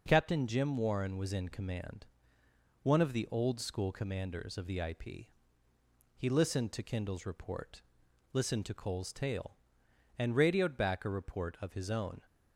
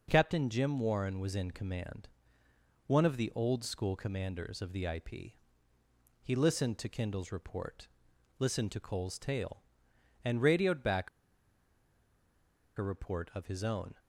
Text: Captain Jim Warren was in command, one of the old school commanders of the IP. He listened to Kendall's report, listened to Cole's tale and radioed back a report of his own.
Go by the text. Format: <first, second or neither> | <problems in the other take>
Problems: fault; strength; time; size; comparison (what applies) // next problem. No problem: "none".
first | pauses between "back" and "a"; strong; at 11.0 s; 1.6 s long